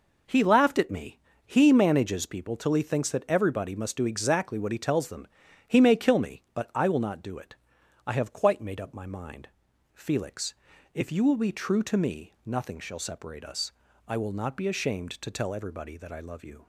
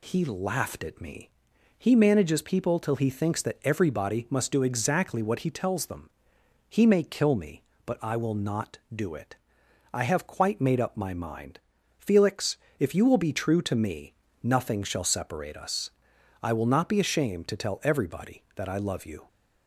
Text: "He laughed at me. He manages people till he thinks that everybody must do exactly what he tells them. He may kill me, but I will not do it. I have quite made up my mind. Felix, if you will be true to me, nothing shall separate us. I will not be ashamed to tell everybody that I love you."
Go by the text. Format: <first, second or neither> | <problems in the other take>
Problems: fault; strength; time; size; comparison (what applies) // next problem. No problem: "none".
neither | none